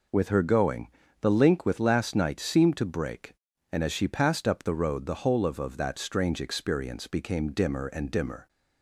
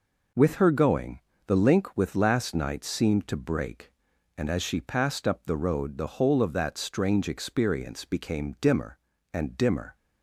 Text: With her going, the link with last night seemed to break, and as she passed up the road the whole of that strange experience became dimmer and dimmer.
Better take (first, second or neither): second